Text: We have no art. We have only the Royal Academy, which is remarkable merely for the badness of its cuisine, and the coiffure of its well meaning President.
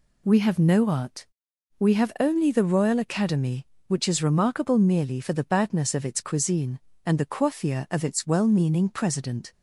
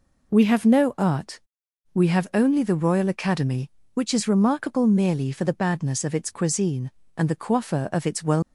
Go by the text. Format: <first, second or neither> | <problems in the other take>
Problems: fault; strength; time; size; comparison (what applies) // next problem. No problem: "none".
first | stops before "meaning President"; at 8.4 s